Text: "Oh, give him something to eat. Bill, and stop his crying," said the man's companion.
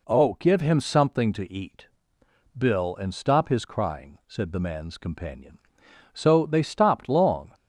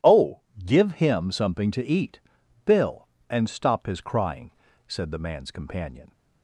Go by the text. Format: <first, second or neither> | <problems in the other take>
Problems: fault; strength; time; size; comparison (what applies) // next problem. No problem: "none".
second | goes on to say "So they stopped long"; from 6.1 s on; 1.4 s long